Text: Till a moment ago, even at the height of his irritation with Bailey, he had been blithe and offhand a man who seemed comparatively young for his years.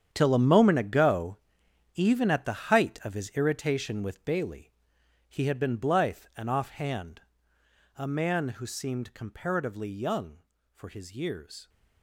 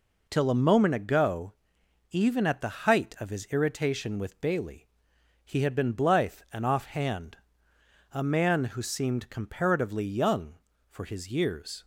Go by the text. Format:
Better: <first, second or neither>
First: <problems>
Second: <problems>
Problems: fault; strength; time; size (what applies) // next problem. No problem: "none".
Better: second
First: gets quieter; strong; throughout; 13.5 dB // pauses between "offhand" and "a"; noticeable; at 7.2 s; 0.76 s long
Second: pauses between "offhand" and "a"; noticeable; at 7.3 s; 0.76 s long